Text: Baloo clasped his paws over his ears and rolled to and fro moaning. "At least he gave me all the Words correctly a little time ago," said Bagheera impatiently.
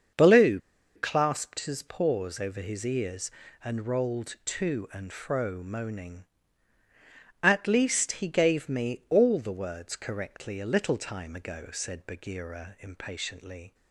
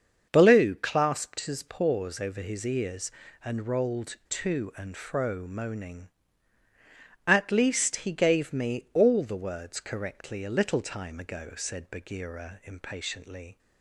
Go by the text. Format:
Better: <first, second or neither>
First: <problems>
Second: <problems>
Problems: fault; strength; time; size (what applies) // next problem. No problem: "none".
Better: second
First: starts louder than the rest; until 1.5 s; 6.5 dB // pauses between "Baloo" and "clasped"; at 0.5 s; 0.36 s long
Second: starts louder than the rest; until 1.3 s; 6.5 dB